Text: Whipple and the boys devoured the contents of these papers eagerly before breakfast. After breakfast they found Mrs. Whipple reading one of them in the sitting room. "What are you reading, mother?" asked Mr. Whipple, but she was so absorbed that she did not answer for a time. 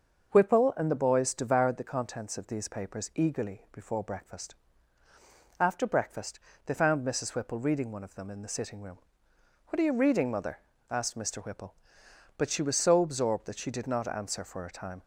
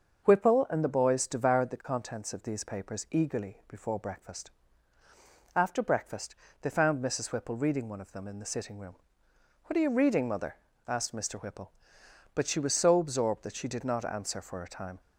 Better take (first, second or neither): neither